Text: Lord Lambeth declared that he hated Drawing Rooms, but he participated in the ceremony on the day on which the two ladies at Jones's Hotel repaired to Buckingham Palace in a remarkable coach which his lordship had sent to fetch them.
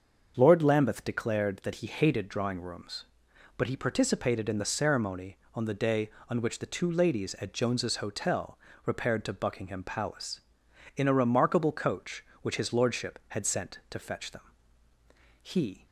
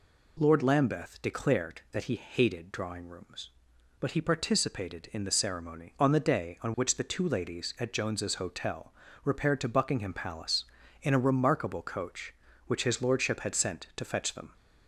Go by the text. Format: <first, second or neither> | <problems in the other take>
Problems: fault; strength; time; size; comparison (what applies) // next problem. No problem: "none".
second | starts louder than the rest; until 1.3 s; 6.5 dB // pauses between "Hotel" and "repaired"; slight; at 8.5 s; 0.28 s long; slight in the second // goes on to say "He"; slight; from 15.4 s on; 0.44 s long